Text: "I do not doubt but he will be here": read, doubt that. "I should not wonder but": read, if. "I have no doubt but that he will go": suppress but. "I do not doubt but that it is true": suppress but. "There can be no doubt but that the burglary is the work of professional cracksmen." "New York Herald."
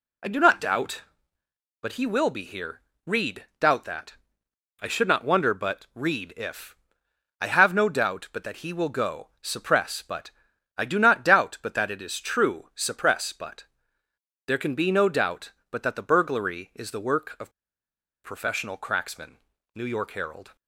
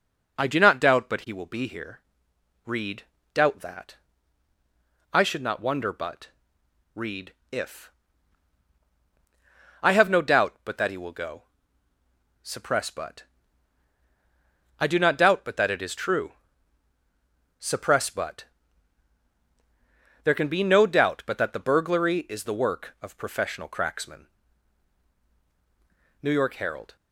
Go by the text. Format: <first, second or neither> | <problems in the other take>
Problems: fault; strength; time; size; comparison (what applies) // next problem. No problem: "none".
second | pauses between "of" and "professional"; noticeable; at 17.5 s; 0.73 s long